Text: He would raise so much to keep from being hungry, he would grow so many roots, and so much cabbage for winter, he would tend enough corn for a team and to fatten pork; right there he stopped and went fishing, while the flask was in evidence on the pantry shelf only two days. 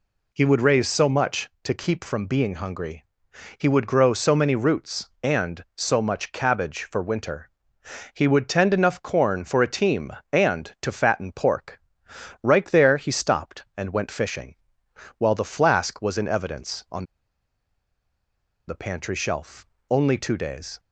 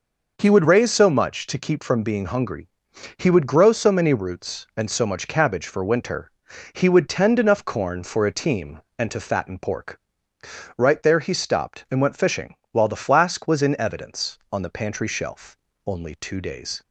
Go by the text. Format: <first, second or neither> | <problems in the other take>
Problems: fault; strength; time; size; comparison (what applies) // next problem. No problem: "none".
second | pauses between "on" and "the"; strong; at 17.0 s; 1.6 s long // pauses between "shelf" and "only"; slight; at 19.6 s; 0.24 s long; slight in the second